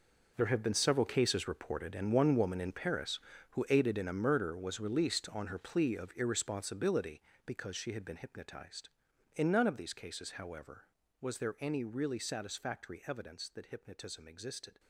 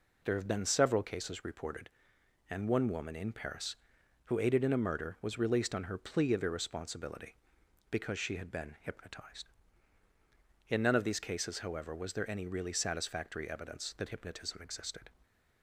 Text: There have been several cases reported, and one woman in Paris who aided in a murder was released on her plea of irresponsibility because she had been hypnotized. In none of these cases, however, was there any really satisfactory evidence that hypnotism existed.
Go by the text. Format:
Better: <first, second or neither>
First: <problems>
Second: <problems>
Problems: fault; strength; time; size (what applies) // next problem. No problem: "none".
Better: second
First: gets quieter; strong; throughout; 14 dB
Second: none